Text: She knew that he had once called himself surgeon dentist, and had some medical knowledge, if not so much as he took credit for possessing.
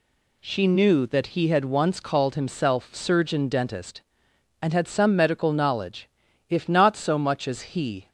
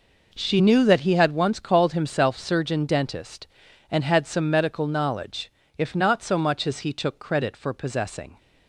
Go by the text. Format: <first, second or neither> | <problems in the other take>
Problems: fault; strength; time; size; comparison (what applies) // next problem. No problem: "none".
second | stops before "took credit for possessing"; at 8.0 s